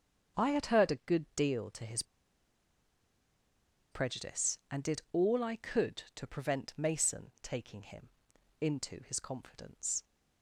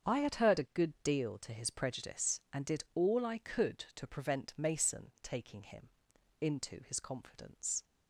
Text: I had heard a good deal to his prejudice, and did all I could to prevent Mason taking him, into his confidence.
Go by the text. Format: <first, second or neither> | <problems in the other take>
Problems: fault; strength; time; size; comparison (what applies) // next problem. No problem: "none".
second | starts louder than the rest; until 1.4 s; 7 dB; strong in the second // pauses between "his" and "prejudice"; strong; at 2.0 s; 1.8 s long